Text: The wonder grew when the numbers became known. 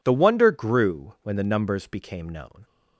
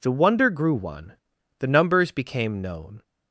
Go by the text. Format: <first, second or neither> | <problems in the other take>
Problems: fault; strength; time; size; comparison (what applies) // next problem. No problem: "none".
first | says "one" for "when"; at 0.7 s